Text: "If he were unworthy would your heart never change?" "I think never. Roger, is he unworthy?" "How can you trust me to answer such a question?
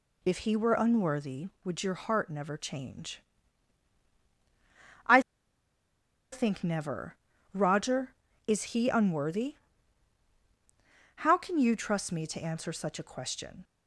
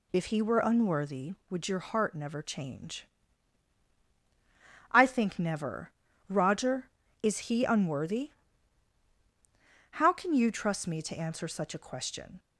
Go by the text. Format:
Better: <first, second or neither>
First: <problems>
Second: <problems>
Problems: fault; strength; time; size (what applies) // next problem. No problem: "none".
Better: second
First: pauses between "I" and "think"; at 5.1 s; 1.1 s long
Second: none